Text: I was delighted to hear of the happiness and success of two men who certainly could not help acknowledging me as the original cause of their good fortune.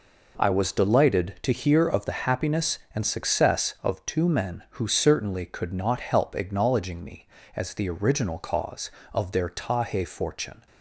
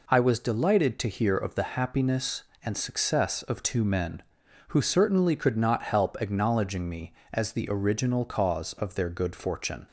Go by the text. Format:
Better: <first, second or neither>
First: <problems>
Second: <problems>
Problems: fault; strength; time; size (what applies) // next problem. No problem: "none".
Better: second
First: says "tahe" for "good"; at 9.4 s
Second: none